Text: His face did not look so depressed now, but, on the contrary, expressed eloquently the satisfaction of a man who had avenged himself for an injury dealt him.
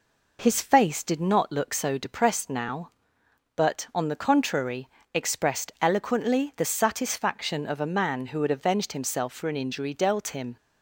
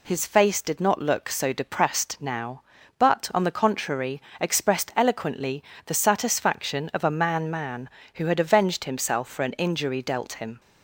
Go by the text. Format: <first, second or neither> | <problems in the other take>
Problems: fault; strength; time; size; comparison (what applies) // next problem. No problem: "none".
first | pauses between "eloquently" and "the"; slight; at 5.6 s; 0.22 s long // says "man" twice; at 7.4 s